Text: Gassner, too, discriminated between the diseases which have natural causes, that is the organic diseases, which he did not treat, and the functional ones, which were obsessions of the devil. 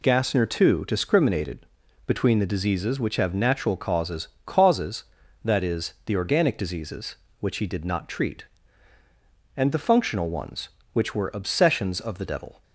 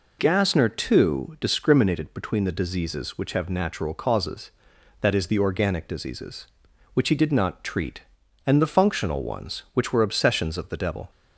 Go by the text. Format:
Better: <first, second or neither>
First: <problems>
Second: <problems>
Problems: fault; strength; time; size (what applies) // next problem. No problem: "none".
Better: second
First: pauses between "discriminated" and "between"; at 1.6 s; 0.42 s long // says "causes" twice; at 4.4 s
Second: none